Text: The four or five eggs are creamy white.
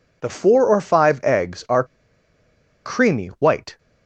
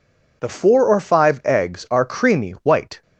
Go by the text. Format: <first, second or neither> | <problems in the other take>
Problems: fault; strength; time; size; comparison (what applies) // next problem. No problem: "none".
second | pauses between "are" and "creamy"; at 1.8 s; 1.0 s long